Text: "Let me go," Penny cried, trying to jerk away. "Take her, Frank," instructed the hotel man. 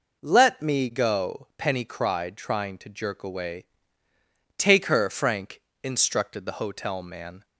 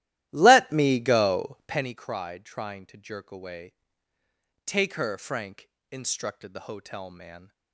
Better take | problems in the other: first | starts louder than the rest; strong; until 1.9 s; 14.5 dB

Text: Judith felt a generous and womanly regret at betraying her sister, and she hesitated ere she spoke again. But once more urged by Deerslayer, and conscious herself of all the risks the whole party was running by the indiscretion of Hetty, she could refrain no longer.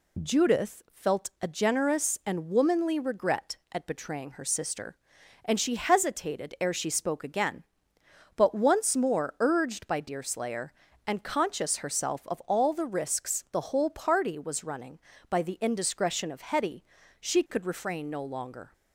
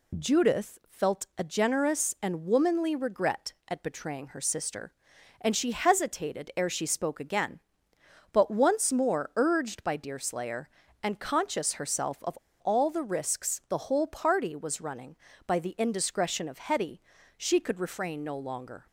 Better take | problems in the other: first | pauses between "of" and "all"; slight; at 12.3 s; 0.22 s long

